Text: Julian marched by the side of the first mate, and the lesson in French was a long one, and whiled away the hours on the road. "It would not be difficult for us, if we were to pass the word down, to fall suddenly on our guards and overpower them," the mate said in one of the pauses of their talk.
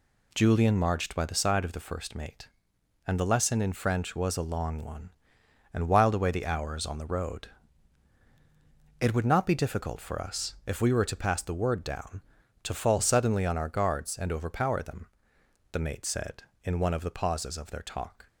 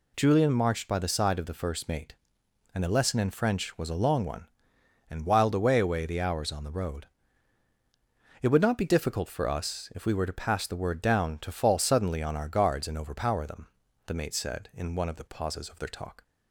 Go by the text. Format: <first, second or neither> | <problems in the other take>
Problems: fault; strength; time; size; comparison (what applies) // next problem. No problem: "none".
first | says "away" twice; at 5.7 s